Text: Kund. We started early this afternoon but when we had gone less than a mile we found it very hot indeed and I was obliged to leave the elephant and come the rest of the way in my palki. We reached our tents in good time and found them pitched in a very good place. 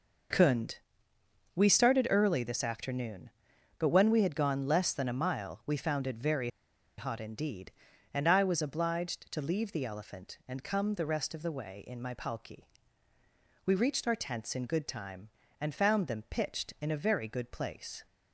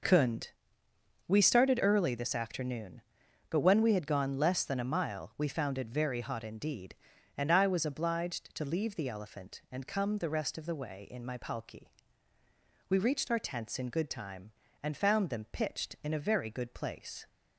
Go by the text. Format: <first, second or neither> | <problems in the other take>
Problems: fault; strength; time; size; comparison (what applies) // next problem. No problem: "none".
second | pauses between "very" and "hot"; noticeable; at 6.4 s; 0.50 s long